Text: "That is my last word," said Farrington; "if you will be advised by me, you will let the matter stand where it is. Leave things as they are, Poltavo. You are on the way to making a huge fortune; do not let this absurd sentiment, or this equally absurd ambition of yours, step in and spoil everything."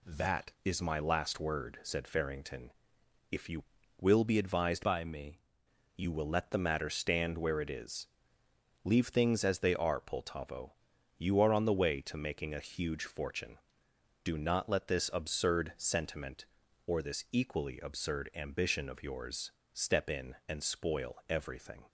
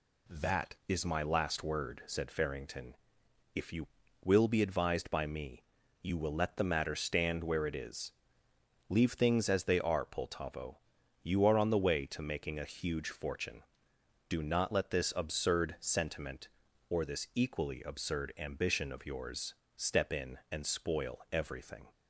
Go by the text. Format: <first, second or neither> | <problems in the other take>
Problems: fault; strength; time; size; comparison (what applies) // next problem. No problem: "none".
second | changes voice from "by" to "me"; from 4.8 to 5.3 s; 0.5 s long